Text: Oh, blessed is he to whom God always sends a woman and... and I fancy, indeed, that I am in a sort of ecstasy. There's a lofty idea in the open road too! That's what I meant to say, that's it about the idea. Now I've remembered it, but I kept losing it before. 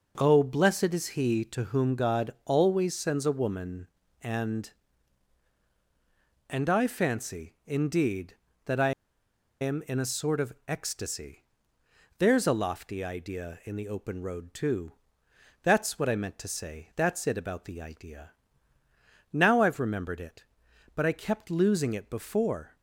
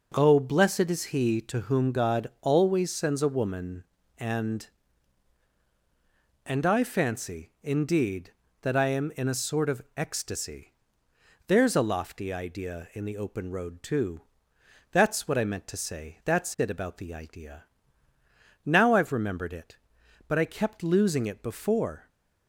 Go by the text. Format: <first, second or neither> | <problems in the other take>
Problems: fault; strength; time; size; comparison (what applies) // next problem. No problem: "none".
second | pauses between "I" and "am"; noticeable; at 8.9 s; 0.68 s long // pauses between "of" and "ecstasy"; slight; at 10.5 s; 0.16 s long; slight in the second